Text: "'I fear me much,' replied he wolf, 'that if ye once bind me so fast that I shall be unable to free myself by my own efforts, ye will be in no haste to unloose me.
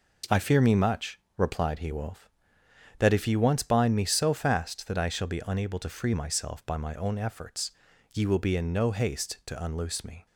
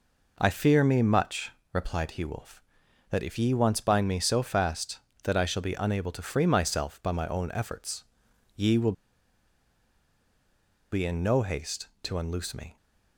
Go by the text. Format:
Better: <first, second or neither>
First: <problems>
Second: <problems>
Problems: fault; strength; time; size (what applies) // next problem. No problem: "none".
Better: first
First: none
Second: pauses between "will" and "be"; strong; at 8.9 s; 1.9 s long